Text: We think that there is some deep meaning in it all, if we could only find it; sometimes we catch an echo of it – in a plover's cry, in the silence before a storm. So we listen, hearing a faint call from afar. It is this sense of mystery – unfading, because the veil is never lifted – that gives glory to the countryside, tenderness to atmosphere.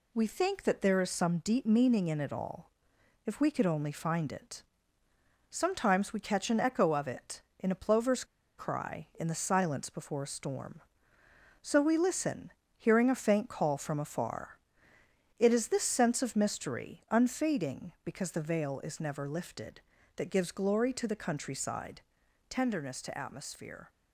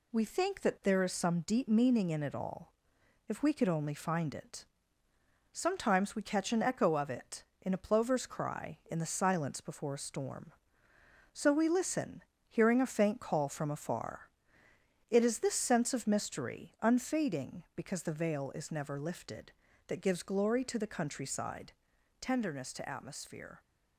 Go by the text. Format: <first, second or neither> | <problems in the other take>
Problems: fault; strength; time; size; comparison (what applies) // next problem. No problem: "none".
second | pauses between "plover's" and "cry"; slight; at 8.2 s; 0.33 s long